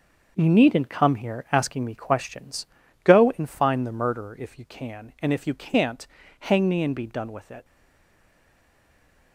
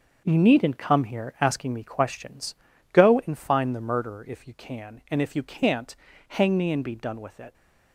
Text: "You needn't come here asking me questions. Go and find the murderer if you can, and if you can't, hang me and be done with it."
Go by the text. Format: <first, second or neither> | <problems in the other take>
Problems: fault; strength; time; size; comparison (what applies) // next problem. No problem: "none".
second | starts louder than the rest; noticeable; until 1.3 s; 6 dB; noticeable in the second // stays silent after the last word; noticeable; from 7.6 s on; 1.7 s long